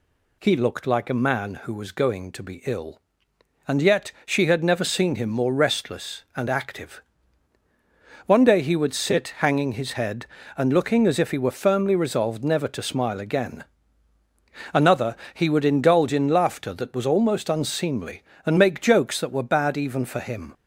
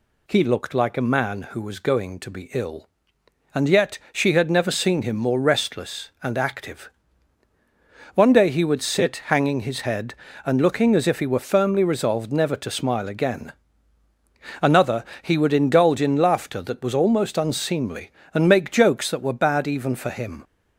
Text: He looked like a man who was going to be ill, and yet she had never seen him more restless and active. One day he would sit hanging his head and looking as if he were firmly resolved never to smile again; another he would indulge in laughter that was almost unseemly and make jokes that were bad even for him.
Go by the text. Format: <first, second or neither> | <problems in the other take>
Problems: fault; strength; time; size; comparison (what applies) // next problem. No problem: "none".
neither | pauses between "another" and "he"; slight; the same in both